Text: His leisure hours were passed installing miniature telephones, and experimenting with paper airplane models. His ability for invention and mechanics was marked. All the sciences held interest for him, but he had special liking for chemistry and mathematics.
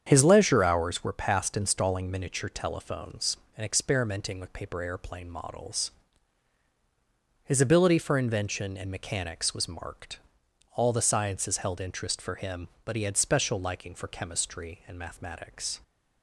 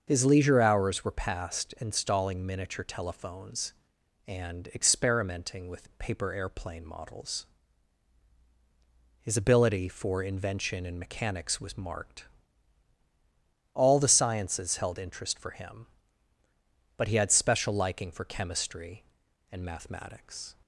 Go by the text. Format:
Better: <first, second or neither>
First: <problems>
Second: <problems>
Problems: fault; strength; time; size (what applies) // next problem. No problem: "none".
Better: neither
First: starts louder than the rest; strong; until 1.0 s; 8 dB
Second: starts louder than the rest; until 1.0 s; 7 dB